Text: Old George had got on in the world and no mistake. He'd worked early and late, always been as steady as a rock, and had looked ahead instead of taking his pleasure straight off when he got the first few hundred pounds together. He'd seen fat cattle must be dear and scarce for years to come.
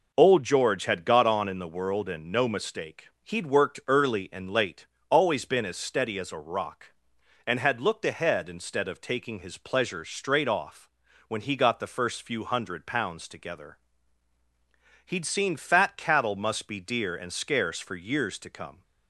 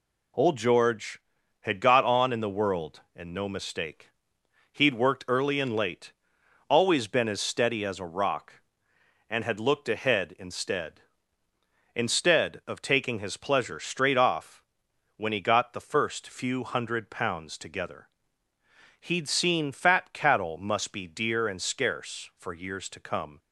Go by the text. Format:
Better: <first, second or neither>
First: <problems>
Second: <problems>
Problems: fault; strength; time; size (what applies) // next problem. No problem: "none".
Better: first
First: pauses between "off" and "when"; at 10.9 s; 0.38 s long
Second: says "instead" twice; at 11.9 s // pauses between "off" and "when"; noticeable; at 14.6 s; 0.54 s long